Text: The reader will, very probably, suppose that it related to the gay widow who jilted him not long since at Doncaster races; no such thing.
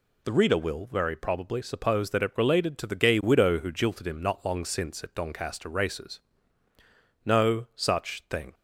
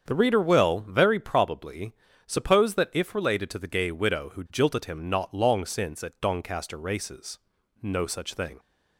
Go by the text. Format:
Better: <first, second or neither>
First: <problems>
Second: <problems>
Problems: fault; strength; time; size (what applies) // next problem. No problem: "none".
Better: first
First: none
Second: starts louder than the rest; strong; until 1.0 s; 7.5 dB // says "if" for "it"; at 2.9 s